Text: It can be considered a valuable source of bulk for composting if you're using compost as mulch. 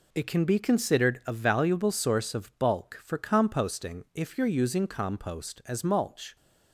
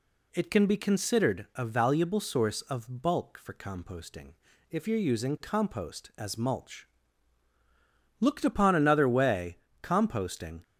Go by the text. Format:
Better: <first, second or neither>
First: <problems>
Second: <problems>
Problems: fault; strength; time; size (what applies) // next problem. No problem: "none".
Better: first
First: none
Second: pauses between "composting" and "if"; slight; at 4.3 s; 0.36 s long // goes on to say "Looked upon another way composting"; strong; from 8.1 s on; 2.4 s long